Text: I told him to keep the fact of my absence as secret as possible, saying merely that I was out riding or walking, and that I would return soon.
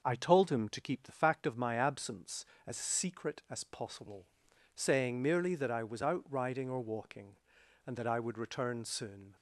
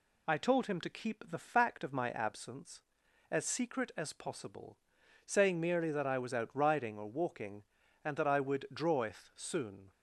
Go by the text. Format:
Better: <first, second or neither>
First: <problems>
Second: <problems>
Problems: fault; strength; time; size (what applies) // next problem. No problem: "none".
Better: first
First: none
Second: says "draweth" for "return"; at 8.7 s